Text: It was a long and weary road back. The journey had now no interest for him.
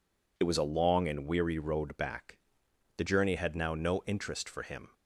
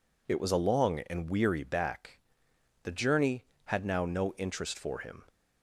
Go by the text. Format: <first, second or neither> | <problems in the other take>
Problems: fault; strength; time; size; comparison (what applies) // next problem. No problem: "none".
first | skips "road"; at 1.6 s